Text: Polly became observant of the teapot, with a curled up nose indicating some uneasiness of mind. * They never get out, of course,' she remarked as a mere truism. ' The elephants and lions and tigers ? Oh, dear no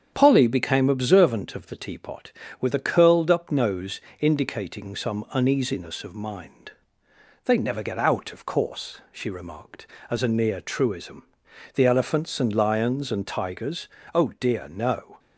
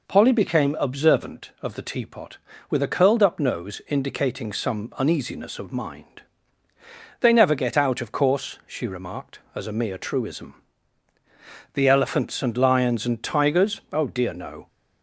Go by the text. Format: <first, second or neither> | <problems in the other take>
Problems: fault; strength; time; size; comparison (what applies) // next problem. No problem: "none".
second | starts louder than the rest; strong; until 1.1 s; 8 dB // pauses between "nose" and "indicating"; slight; at 3.9 s; 0.22 s long // says "near" for "mere"; at 10.2 s